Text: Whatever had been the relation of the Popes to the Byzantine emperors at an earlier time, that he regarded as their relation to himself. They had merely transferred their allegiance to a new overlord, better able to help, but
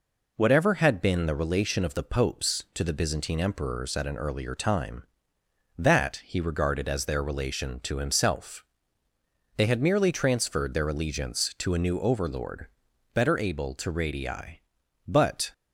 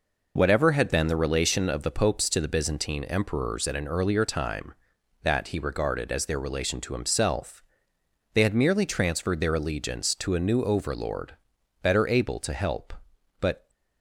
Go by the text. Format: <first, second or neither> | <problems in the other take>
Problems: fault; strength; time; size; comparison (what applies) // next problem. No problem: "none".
second | says "radii" for "help"; at 13.9 s